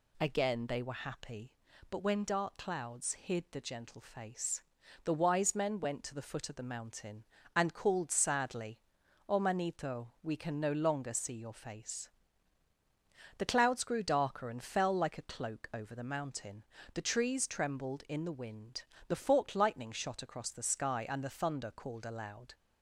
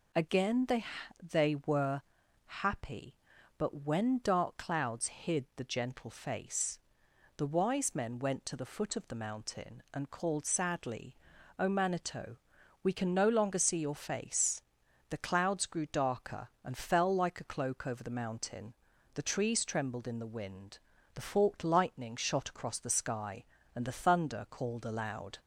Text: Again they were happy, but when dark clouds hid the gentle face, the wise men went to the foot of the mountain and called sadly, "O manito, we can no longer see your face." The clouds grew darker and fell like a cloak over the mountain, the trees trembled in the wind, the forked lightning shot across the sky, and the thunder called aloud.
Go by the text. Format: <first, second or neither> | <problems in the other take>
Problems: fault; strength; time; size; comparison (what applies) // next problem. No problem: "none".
first | says "they" twice; at 1.2 s // pauses between "were" and "happy"; noticeable; at 2.0 s; 0.46 s long